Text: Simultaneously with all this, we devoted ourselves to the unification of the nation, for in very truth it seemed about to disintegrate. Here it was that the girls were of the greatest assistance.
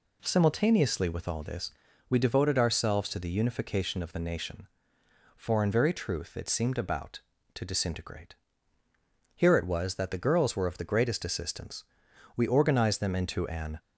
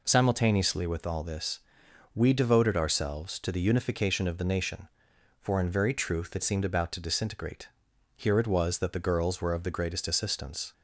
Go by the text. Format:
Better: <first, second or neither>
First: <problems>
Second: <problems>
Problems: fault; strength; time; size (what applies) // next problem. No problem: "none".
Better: second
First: goes on to say "We organized them into an"; from 12.3 s on; 1.4 s long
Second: none